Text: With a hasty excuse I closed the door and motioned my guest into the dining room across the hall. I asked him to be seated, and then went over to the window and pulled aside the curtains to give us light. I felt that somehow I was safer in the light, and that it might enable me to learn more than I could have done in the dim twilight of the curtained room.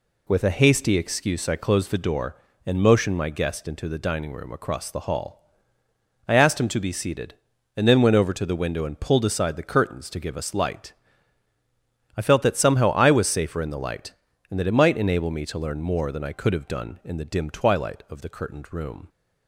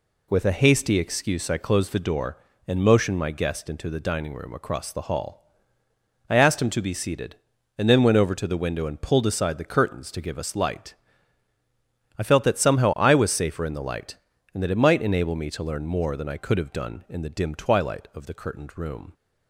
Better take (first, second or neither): neither